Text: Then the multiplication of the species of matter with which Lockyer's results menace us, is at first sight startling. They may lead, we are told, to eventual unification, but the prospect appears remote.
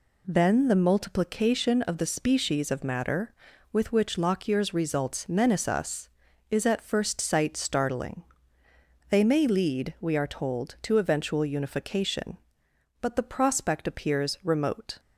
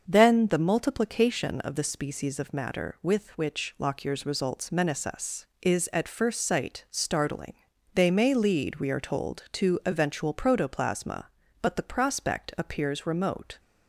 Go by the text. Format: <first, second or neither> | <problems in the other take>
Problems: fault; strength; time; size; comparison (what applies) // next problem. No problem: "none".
first | starts louder than the rest; until 1.0 s; 6 dB // says "protoplasma" for "unification"; at 10.3 s